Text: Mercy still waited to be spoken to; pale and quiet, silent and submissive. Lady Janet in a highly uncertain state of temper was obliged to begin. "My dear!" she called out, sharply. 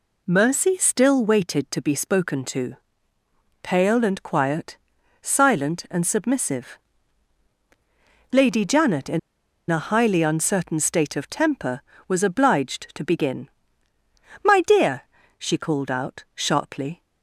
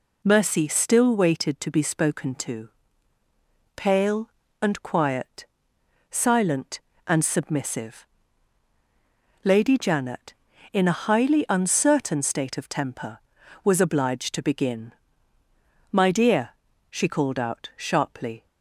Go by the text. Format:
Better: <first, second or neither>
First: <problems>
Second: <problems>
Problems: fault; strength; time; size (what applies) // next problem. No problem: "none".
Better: second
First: pauses between "in" and "a"; noticeable; at 9.1 s; 0.49 s long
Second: none